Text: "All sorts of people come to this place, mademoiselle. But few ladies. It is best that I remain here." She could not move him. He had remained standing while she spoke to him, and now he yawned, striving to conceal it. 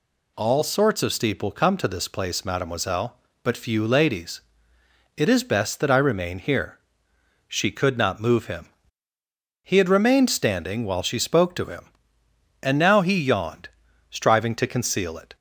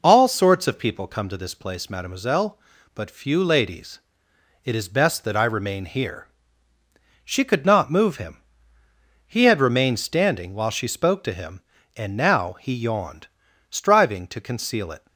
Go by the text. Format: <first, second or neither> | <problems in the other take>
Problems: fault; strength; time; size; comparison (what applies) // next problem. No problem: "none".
second | says "steeple" for "people"; at 1.1 s